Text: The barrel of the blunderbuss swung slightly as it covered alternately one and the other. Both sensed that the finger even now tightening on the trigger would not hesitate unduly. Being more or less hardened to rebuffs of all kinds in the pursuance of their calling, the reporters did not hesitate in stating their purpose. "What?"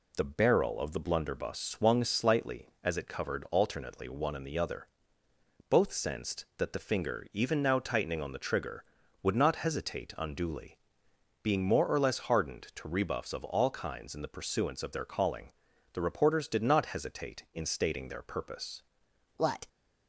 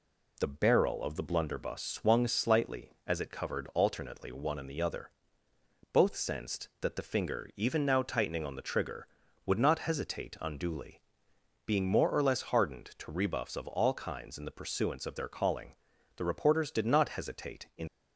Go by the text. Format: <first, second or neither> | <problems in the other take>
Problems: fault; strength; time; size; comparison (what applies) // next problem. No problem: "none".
first | stops before "stating their purpose What"; at 17.8 s